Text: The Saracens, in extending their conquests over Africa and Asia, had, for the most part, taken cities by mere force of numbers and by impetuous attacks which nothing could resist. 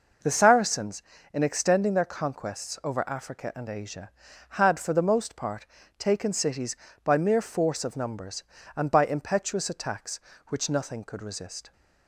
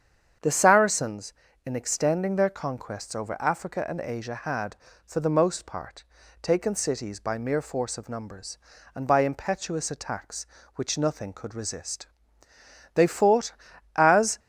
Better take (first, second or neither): first